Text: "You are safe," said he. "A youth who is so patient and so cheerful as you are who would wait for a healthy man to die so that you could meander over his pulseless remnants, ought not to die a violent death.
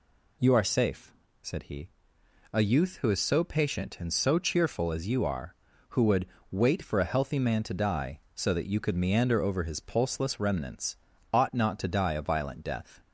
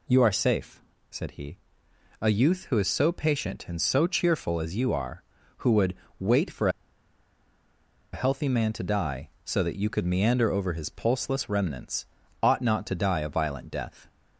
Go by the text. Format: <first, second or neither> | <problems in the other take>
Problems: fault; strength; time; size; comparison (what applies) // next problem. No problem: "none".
first | pauses between "would" and "wait"; slight; at 5.9 s; 0.22 s long; slight in the first // pauses between "for" and "a"; strong; at 6.6 s; 1.4 s long